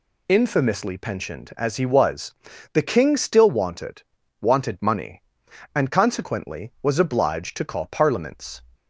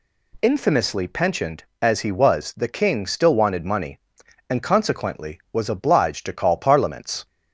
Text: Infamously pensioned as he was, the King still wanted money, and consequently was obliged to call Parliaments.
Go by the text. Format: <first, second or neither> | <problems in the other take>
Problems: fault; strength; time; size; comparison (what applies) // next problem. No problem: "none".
second | says "wanted" twice; at 4.4 s